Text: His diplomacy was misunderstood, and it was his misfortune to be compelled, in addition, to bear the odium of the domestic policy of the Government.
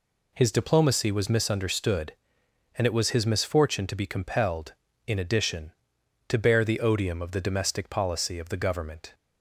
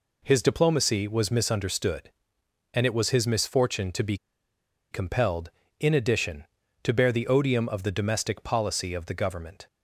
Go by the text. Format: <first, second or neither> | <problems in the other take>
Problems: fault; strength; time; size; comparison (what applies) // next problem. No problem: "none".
first | pauses between "be" and "compelled"; noticeable; at 4.1 s; 0.76 s long